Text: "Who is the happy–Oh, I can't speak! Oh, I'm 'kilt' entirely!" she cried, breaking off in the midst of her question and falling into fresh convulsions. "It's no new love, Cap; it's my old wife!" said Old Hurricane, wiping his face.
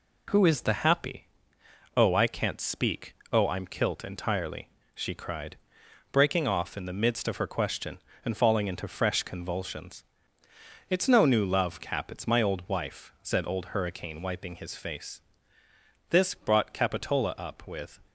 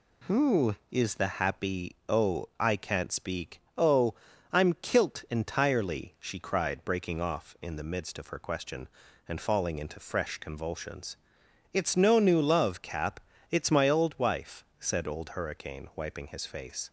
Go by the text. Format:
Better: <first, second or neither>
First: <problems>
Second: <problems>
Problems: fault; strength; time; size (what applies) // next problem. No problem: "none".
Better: second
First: goes on to say "This brought Capitola up with"; strong; from 16.1 s on; 1.8 s long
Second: none